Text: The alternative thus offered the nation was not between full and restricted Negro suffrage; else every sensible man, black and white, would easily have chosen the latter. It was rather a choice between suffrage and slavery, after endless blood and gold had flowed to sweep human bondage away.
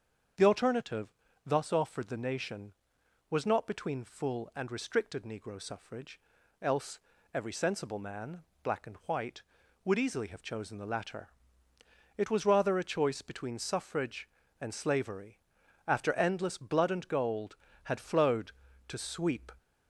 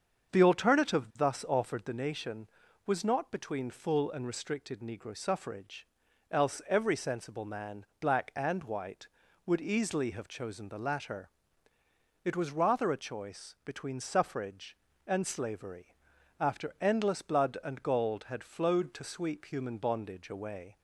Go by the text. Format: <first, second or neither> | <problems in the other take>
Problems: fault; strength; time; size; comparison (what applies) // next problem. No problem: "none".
second | starts louder than the rest; strong; until 1.7 s; 7.5 dB; also in the second // pauses between "alternative" and "thus"; at 1.0 s; 0.38 s long // pauses between "else" and "every"; slight; at 6.9 s; 0.36 s long // stops before "human bondage away"; at 19.5 s